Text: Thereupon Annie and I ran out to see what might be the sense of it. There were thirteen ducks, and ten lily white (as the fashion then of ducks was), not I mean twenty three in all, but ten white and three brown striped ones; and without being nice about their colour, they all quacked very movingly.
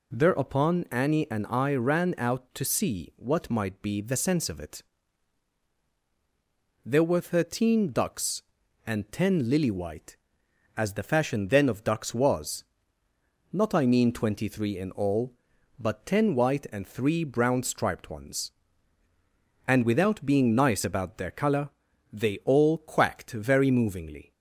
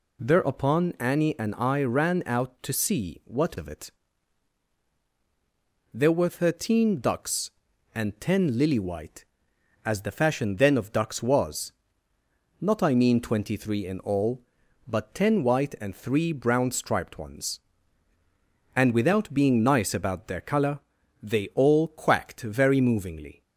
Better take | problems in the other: first | skips "might be the sense"; at 3.5 s

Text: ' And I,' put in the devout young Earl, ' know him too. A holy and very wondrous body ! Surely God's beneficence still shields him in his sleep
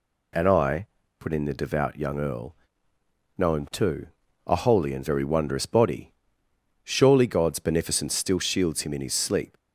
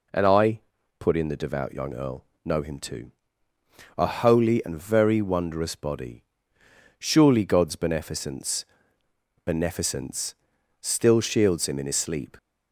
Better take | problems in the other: first | says "beneficence" twice; at 9.4 s

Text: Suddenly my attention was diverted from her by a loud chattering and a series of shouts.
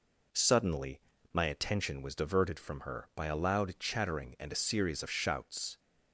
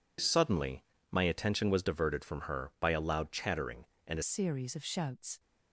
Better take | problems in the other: first | pauses between "Suddenly" and "my"; slight; at 0.8 s; 0.28 s long; slight in the first // changes voice at "series"; from 4.2 s on; 1.1 s long

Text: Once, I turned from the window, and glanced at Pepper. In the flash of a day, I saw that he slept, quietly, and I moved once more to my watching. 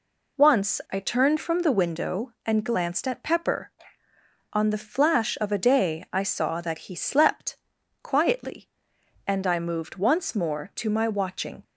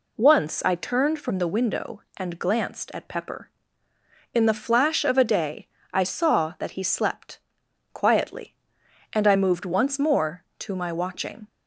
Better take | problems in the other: second | says "On" for "In"; at 4.5 s

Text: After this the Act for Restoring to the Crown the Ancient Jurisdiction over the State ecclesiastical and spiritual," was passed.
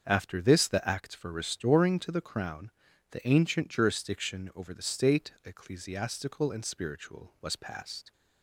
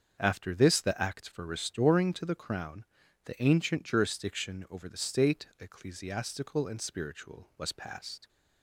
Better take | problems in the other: neither | starts louder than the rest; the same in both // pauses between "Crown" and "the"; the same in both

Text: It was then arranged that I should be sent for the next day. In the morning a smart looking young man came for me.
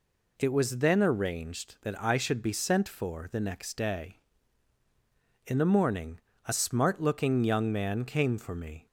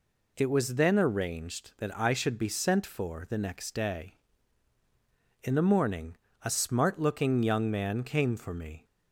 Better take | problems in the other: neither | pauses between "morning" and "a"; slight; the same in both

